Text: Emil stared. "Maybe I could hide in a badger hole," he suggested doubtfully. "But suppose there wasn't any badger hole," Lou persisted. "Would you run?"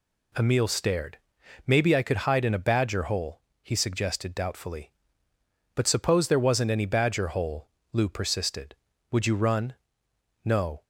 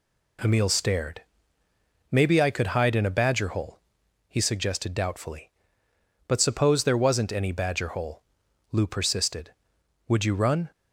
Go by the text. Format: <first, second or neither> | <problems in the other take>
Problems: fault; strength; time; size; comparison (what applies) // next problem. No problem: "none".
second | goes on to say "No"; slight; from 10.4 s on; 0.40 s long